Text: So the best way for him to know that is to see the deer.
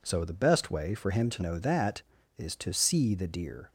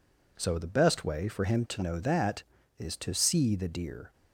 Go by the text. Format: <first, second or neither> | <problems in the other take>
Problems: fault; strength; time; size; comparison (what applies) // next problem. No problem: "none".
neither | none